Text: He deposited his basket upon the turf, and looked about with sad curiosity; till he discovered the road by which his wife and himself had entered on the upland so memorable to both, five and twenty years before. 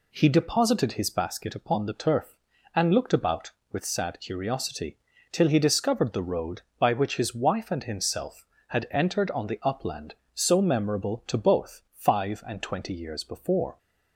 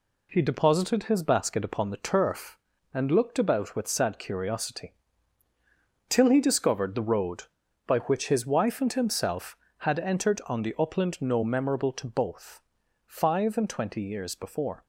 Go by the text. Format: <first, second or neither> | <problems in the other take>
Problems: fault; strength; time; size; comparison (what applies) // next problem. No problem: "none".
first | says "no" for "so"; at 11.2 s